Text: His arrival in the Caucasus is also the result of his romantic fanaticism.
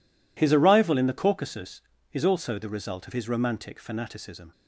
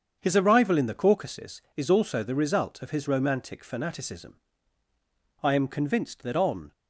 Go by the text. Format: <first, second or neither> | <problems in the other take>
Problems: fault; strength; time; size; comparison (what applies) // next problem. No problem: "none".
first | starts louder than the rest; strong; until 1.2 s; 7.5 dB // goes on to say "I am convinced that on"; noticeable; from 5.4 s on; 1.2 s long